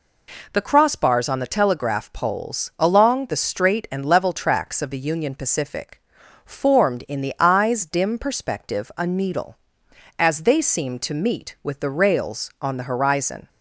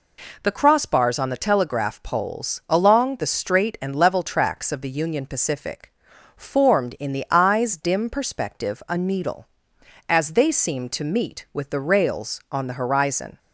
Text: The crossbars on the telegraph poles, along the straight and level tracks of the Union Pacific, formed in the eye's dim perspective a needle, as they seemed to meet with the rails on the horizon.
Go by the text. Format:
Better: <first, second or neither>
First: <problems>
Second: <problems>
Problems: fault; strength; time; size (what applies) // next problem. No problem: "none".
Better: neither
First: none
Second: none